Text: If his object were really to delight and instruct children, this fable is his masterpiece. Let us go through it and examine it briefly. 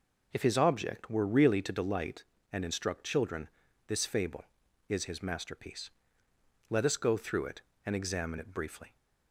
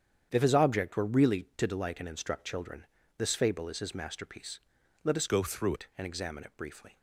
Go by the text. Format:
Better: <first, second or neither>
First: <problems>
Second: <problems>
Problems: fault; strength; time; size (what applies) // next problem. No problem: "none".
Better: first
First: none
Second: starts louder than the rest; strong; until 1.3 s; 8.5 dB // changes voice from "go" to "through"; from 5.2 to 5.7 s; 0.5 s long